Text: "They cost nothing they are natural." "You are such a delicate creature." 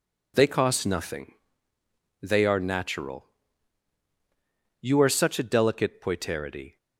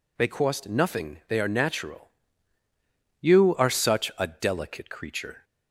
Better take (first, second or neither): second